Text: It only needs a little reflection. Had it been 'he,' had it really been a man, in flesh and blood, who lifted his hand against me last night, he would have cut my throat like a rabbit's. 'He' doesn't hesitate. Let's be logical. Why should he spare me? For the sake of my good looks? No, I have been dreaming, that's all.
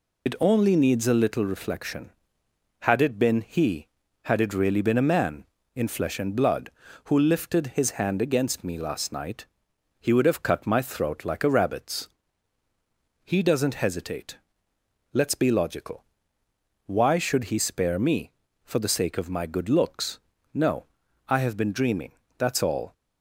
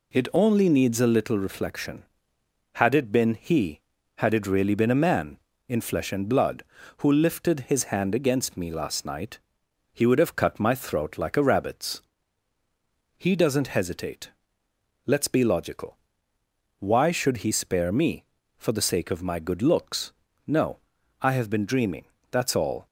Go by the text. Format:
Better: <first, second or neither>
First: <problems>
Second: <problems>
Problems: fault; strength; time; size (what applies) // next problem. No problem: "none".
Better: second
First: loses the start of "It"; at 0.2 s; 70 ms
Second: none